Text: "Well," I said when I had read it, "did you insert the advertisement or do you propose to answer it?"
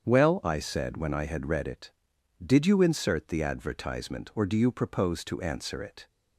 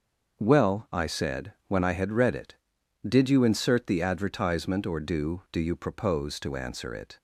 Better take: first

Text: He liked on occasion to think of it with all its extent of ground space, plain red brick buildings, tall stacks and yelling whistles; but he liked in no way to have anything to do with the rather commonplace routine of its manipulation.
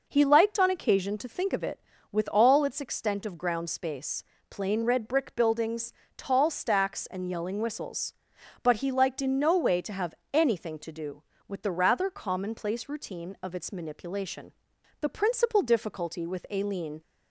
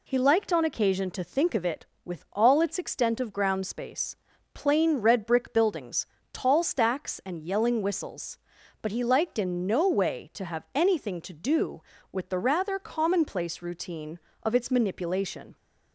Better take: second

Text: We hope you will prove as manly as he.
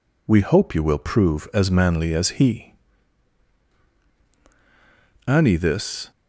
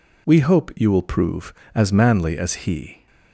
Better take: second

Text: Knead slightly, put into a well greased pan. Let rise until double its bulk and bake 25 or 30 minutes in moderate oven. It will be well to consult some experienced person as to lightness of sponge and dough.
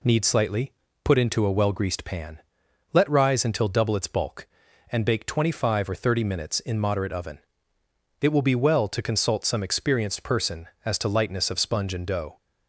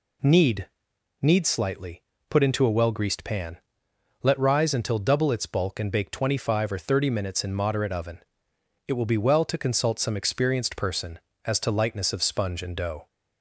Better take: first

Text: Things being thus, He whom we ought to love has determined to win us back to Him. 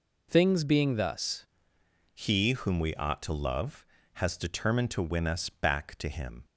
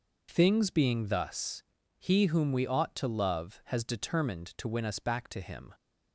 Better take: second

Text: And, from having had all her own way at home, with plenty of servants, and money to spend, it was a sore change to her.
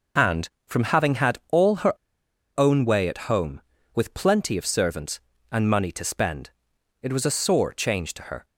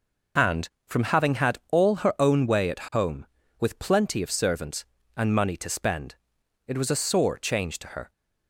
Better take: second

